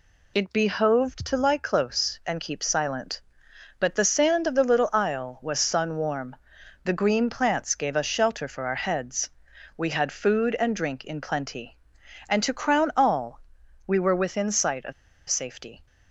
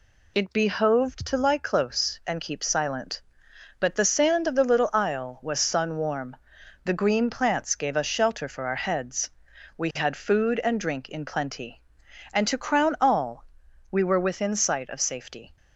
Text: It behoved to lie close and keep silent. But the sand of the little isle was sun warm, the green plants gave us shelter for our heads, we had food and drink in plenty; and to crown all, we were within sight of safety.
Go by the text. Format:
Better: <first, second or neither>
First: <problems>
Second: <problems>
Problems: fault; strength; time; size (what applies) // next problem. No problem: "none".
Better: second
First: pauses between "of" and "safety"; at 14.9 s; 0.36 s long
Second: none